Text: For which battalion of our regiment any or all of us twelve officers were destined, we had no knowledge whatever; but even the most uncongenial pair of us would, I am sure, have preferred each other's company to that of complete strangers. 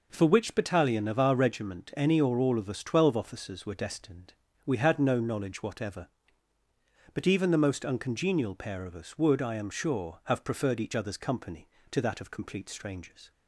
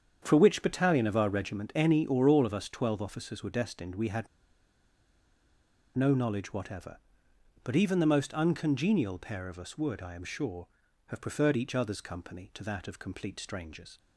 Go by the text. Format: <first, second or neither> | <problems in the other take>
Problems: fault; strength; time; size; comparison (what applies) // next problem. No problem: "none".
first | starts louder than the rest; strong; until 1.2 s; 8 dB // pauses between "had" and "no"; strong; at 4.2 s; 1.7 s long